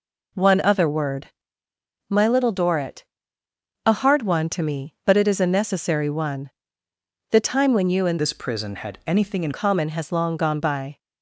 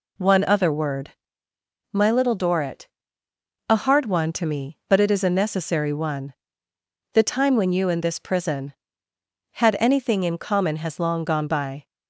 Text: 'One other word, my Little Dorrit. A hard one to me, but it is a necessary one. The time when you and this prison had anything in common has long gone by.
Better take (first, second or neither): second